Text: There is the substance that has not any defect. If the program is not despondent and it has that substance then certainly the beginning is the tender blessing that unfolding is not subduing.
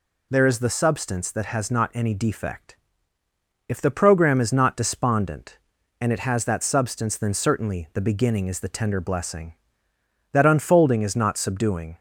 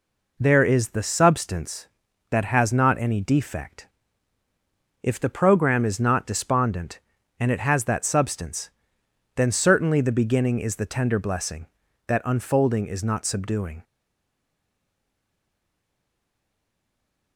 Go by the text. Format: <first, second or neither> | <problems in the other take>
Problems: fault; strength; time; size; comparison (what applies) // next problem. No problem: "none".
first | pauses between "substance" and "then"; noticeable; at 8.6 s; 0.64 s long // stays silent after the last word; strong; from 13.8 s on; 3.5 s long